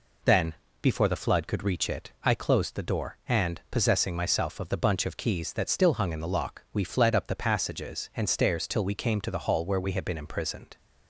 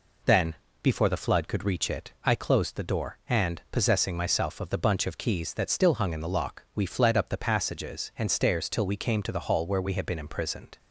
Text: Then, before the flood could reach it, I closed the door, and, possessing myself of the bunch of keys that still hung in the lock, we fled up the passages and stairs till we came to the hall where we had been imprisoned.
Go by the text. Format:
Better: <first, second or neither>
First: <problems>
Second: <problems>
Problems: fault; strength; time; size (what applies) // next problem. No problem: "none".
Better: neither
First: none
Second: none